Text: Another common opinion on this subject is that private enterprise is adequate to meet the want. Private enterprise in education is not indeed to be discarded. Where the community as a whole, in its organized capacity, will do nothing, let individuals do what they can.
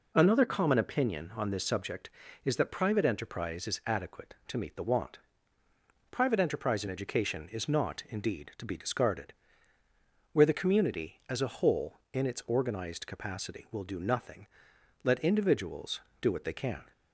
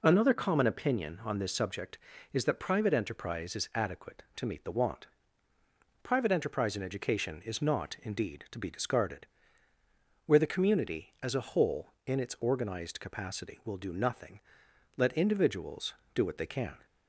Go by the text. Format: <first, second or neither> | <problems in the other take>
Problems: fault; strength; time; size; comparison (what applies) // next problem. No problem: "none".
neither | none